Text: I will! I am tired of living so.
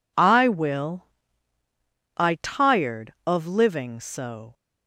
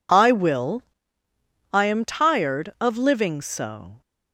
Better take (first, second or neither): second